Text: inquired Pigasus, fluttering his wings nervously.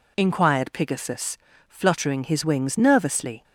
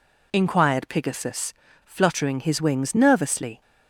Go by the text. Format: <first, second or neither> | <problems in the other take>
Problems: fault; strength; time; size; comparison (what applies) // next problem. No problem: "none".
neither | none